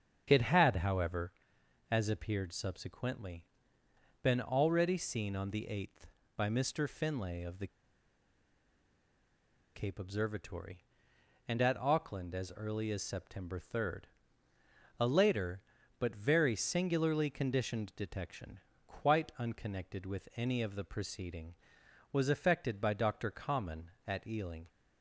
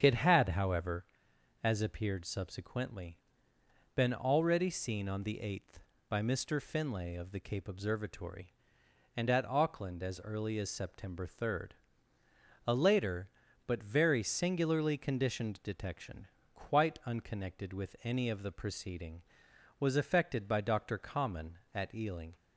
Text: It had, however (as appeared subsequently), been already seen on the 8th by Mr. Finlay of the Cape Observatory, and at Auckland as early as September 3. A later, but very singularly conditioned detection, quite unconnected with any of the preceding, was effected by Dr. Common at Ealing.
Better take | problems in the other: second | starts louder than the rest; strong; until 1.2 s; 7.5 dB; strong in the second // pauses between "the" and "Cape"; strong; at 7.6 s; 2.0 s long

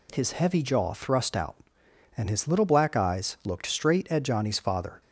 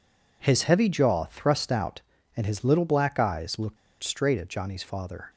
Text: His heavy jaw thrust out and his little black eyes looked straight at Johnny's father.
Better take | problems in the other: first | pauses between "looked" and "straight"; slight; at 3.7 s; 0.25 s long

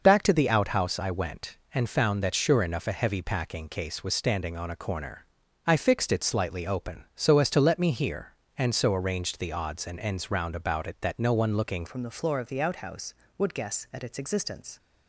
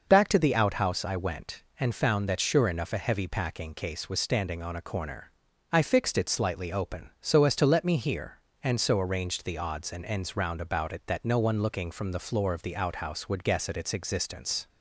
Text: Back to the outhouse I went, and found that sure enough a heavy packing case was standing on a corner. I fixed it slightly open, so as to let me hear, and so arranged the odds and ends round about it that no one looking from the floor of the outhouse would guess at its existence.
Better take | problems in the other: second | changes voice at "from"; from 11.8 s on; 2.9 s long

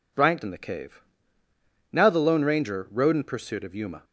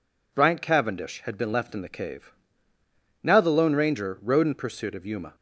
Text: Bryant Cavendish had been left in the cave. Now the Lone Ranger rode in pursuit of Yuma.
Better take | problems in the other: second | skips "Cavendish had been left"; at 0.4 s

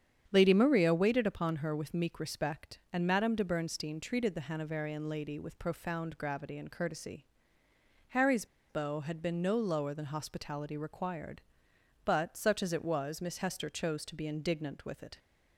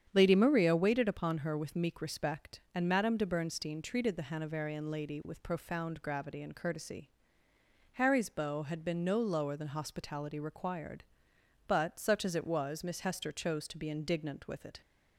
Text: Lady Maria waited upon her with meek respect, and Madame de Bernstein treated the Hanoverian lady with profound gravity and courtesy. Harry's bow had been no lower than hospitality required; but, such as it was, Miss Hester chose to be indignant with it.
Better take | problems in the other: second | starts louder than the rest; strong; until 1.3 s; 8.5 dB; strong in the second // pauses between "Harry's" and "bow"; slight; at 8.4 s; 0.24 s long

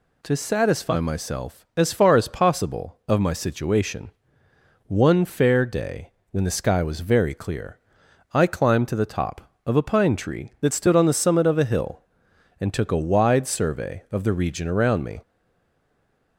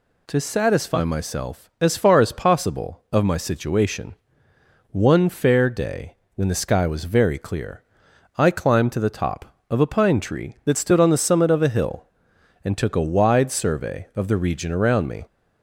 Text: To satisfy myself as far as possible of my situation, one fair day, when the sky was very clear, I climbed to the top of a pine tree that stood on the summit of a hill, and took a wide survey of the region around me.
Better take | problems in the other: second | stays silent after the last word; from 15.2 s on; 1.1 s long

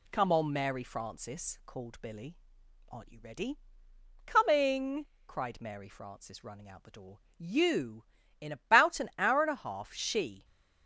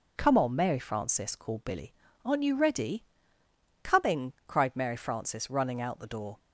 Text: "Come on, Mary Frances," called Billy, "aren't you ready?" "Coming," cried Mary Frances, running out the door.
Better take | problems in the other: second | goes on to say "you In about an hour and a half she"; strong; from 7.3 s on; 3.0 s long

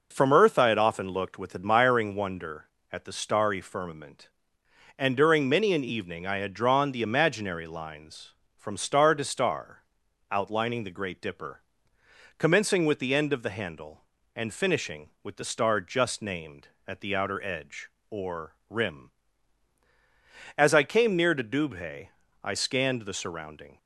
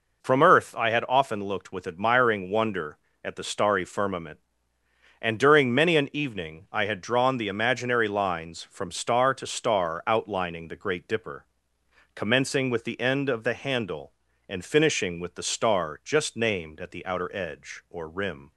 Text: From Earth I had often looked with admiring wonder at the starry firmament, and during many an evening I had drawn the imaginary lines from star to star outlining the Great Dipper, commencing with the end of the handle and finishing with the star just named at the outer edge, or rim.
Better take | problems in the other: second | pauses between "star" and "outlining"; noticeable; at 9.8 s; 0.46 s long // goes on to say "As I came near to Dubhe I scanned the surrounding"; strong; from 20.5 s on; 3.2 s long

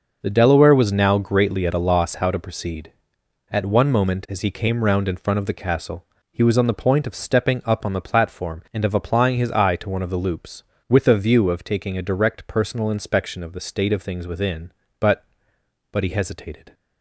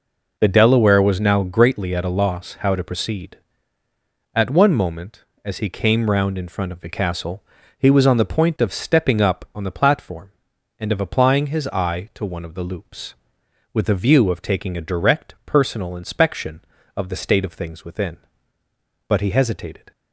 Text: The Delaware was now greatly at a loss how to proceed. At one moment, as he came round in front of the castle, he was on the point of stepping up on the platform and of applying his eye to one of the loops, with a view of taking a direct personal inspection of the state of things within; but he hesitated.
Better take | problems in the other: second | says "but" twice; at 15.8 s

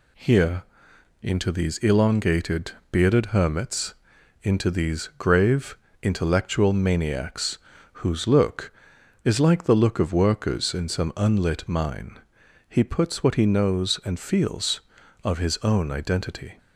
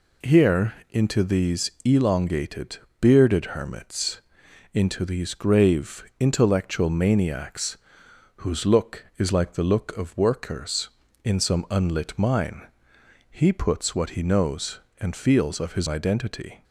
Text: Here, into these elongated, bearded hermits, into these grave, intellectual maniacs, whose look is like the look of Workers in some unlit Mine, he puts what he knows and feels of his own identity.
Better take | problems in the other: first | skips "own"; at 15.8 s

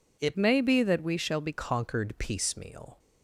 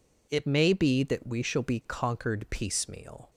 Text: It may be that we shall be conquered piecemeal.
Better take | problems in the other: second | changes voice from "may" to "be"; from 0.3 to 1.5 s; 1.2 s long

